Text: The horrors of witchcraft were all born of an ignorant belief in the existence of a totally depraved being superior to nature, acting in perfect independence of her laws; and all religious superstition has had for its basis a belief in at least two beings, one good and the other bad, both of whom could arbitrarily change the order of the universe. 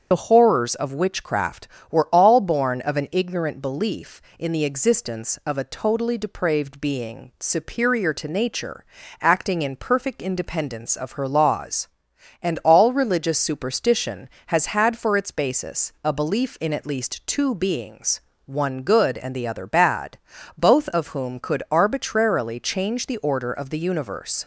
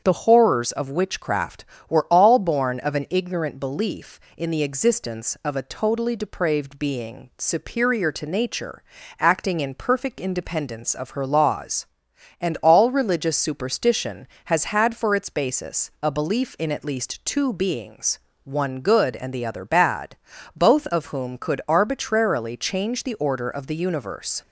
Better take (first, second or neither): second